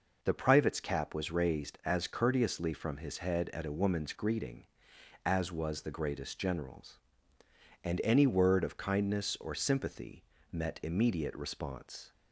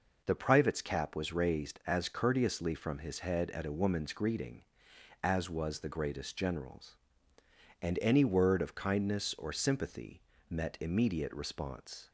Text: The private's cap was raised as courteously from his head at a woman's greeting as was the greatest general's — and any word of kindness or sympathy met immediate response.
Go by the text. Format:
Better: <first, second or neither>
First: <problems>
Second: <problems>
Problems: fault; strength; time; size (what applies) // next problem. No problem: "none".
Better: neither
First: pauses between "sympathy" and "met"; slight; at 10.2 s; 0.28 s long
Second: pauses between "sympathy" and "met"; slight; at 10.2 s; 0.28 s long